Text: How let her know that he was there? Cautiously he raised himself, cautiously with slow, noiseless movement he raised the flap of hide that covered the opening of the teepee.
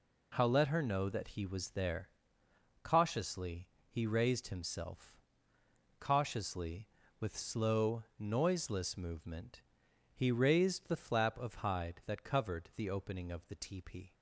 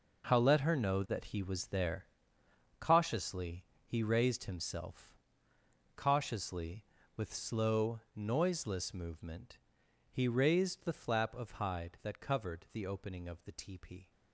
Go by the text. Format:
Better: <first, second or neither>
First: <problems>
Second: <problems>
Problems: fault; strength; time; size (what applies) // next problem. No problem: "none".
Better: first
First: pauses between "Cautiously" and "he"; slight; at 3.6 s; 0.22 s long // pauses between "movement" and "he"; noticeable; at 9.5 s; 0.56 s long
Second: gets quieter; strong; throughout; 12 dB // pauses between "Cautiously" and "he"; slight; at 3.6 s; 0.22 s long // pauses between "movement" and "he"; noticeable; at 9.5 s; 0.56 s long